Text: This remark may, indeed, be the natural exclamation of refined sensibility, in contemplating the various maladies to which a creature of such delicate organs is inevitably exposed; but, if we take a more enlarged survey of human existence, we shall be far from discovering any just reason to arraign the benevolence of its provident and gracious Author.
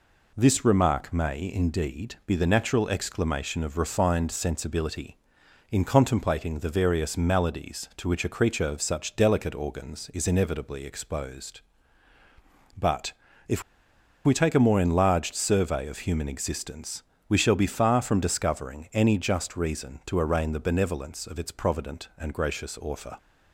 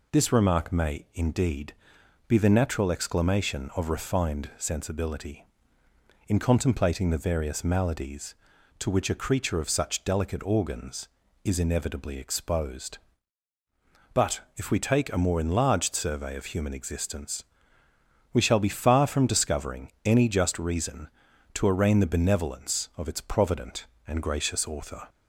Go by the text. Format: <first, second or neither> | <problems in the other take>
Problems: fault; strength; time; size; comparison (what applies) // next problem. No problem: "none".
second | pauses between "if" and "we"; noticeable; at 13.6 s; 0.63 s long